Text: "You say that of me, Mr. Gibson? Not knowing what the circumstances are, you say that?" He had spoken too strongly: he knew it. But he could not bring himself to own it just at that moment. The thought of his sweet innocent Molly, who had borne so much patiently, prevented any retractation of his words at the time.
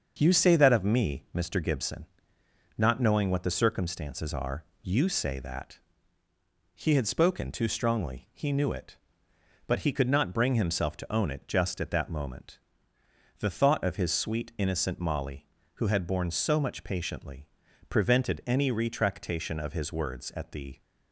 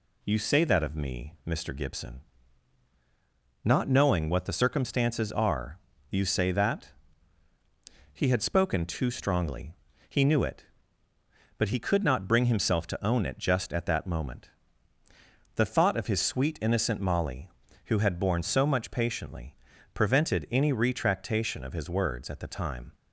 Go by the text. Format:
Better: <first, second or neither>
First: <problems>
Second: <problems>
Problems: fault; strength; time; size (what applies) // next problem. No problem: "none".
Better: second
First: starts louder than the rest; until 1.2 s; 6.5 dB // stops before "time"; at 20.7 s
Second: none